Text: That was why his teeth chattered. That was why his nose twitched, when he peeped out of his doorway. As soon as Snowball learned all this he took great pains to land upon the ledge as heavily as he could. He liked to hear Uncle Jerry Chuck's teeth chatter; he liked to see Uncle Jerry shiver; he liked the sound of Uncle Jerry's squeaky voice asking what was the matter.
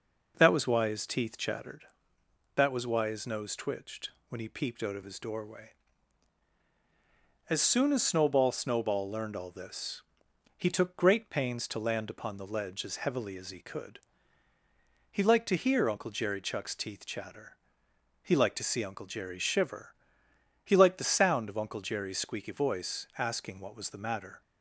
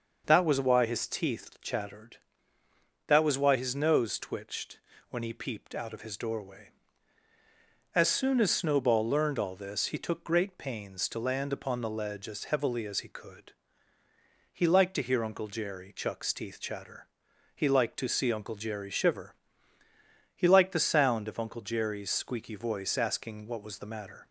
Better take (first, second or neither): second